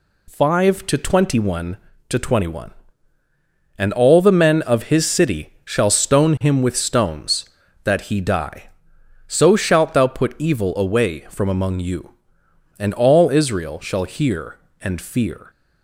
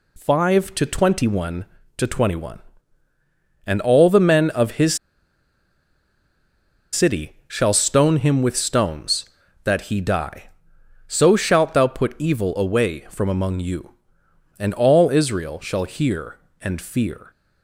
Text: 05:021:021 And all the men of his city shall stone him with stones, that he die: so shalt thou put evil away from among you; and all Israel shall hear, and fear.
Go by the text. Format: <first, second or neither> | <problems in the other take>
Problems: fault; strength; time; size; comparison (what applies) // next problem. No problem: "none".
first | pauses between "his" and "city"; strong; at 4.9 s; 1.9 s long // pauses between "city" and "shall"; slight; at 7.3 s; 0.16 s long; slight in the first